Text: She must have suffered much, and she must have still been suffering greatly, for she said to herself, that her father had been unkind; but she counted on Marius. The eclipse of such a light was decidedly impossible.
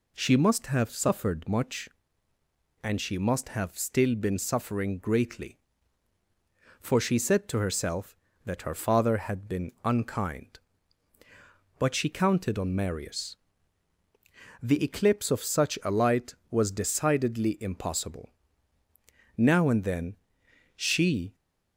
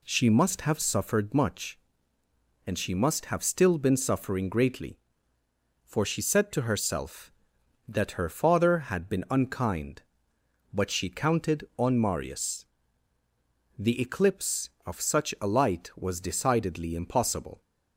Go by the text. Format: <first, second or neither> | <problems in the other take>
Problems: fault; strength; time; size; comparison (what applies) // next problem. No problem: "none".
second | goes on to say "Now and then she"; strong; from 19.4 s on; 1.9 s long